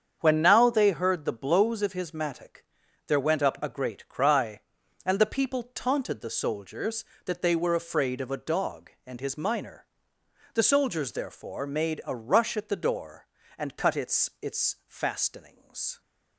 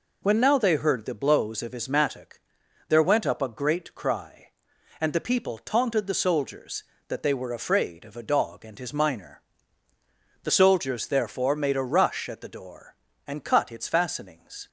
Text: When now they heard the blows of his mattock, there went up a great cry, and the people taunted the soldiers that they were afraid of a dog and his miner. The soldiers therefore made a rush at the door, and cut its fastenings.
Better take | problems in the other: second | starts louder than the rest; strong; until 1.2 s; 7.5 dB // says "its" twice; at 14.3 s

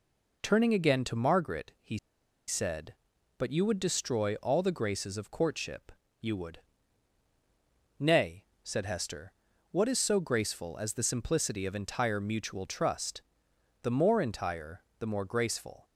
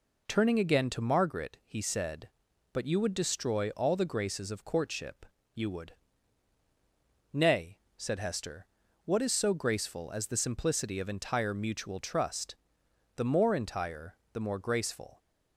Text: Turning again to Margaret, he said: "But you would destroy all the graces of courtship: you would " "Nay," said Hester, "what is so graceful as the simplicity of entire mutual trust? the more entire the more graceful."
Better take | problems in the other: second | pauses between "he" and "said"; noticeable; at 1.9 s; 0.50 s long // pauses between "entire" and "the"; slight; at 14.8 s; 0.16 s long; slight in the second

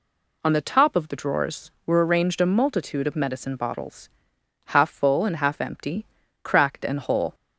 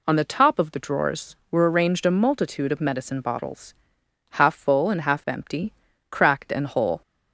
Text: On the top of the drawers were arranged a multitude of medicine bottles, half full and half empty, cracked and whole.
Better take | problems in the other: neither | none

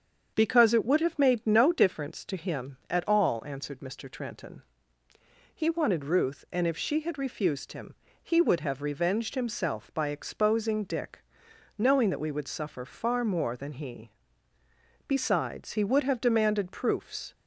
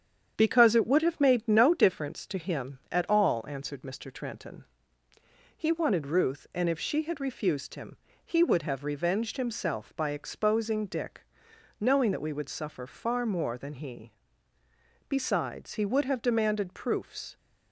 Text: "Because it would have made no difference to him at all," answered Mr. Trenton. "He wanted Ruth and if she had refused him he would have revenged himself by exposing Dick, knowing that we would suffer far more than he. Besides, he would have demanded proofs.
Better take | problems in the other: first | gets quieter; throughout; 3.5 dB // starts louder than the rest; strong; until 1.3 s; 8.5 dB; strong in the first // pauses between "him" and "he"; slight; at 7.9 s; 0.30 s long; slight in the first

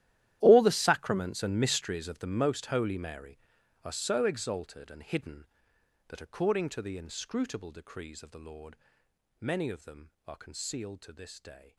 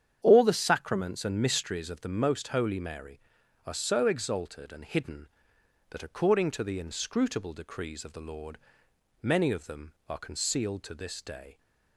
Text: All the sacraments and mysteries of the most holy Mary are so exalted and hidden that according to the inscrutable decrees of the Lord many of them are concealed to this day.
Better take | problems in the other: second | gets quieter; strong; throughout; 19 dB // starts louder than the rest; strong; until 1.4 s; 12.5 dB; strong in the second // pauses between "Lord" and "many"; noticeable; at 8.7 s; 0.62 s long; noticeable in the second

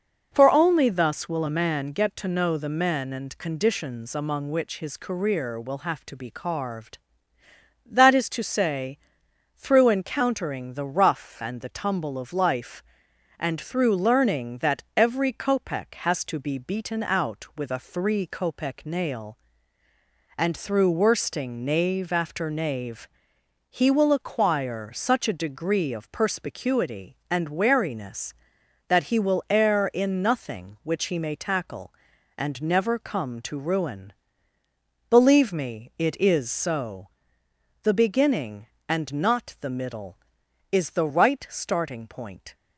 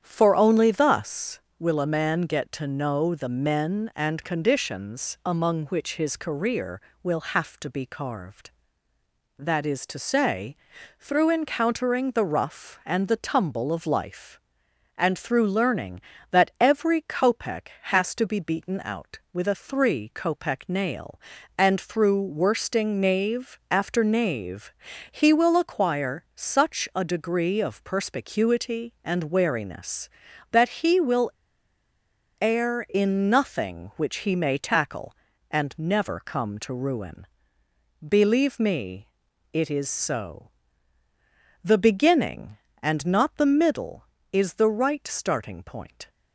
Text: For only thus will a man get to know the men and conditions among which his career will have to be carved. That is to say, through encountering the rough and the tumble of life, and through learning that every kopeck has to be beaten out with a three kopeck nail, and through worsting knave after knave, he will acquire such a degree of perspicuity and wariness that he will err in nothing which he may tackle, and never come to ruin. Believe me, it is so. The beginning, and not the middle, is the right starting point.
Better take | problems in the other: first | starts louder than the rest; strong; until 1.0 s; 9 dB // pauses between "will" and "err"; at 31.3 s; 1.0 s long

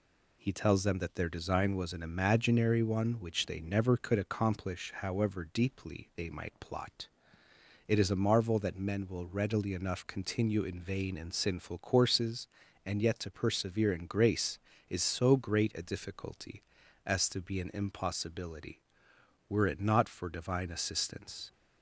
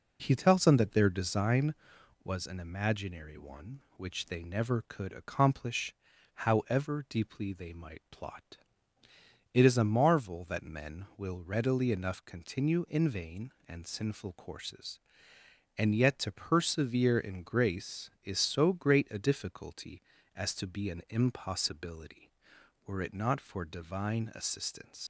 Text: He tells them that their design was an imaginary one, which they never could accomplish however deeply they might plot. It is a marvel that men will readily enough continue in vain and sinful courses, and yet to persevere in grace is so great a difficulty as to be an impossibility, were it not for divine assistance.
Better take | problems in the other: first | pauses between "accomplish" and "however"; at 5.9 s; 0.40 s long // leaves "assistance" unfinished; at 25.0 s; 80 ms

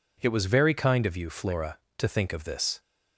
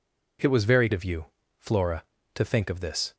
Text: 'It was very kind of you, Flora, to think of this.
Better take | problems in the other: first | skips "kind"; at 0.9 s

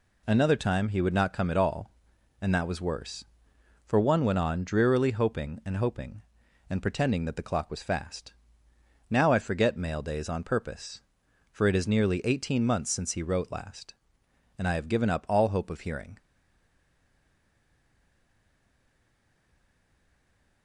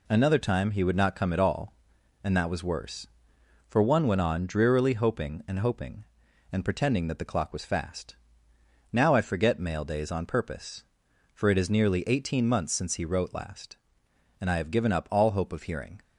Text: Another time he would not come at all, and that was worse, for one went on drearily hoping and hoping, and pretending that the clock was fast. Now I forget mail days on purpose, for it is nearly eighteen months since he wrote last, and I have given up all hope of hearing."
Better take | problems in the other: second | stays silent after the last word; strong; from 16.1 s on; 4.5 s long

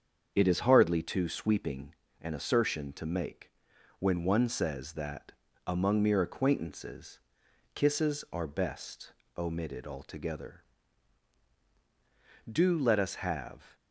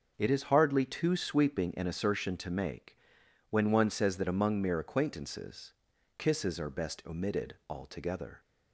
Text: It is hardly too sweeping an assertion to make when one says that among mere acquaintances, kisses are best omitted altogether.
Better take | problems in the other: second | starts louder than the rest; strong; until 1.3 s; 7 dB // pauses between "sweeping" and "an"; slight; at 1.9 s; 0.28 s long // pauses between "make" and "when"; noticeable; at 3.5 s; 0.48 s long; noticeable in the second // pauses between "that" and "among"; slight; at 5.3 s; 0.34 s long // pauses between "best" and "omitted"; slight; at 9.1 s; 0.24 s long // goes on to say "Do let us have"; noticeable; from 12.4 s on; 1.2 s long

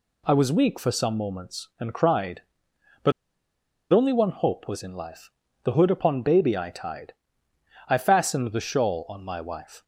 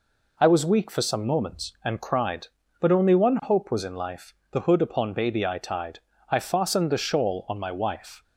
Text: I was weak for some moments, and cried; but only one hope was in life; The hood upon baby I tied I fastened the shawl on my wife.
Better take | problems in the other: second | pauses between "but" and "only"; noticeable; at 3.1 s; 0.80 s long // pauses between "tied" and "I"; noticeable; at 7.1 s; 0.78 s long; slight in the second

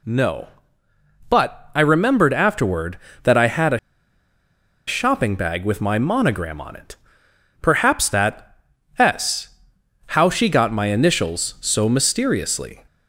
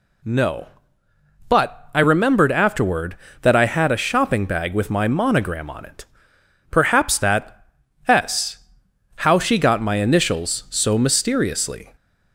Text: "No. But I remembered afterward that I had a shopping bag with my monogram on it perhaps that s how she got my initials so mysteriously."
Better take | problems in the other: second | pauses between "a" and "shopping"; at 3.7 s; 1.0 s long // pauses between "it" and "perhaps"; noticeable; at 6.9 s; 0.64 s long; noticeable in the second // pauses between "that" and "s"; at 8.5 s; 0.44 s long; also in the second // pauses between "s" and "how"; noticeable; at 9.4 s; 0.64 s long; noticeable in the second

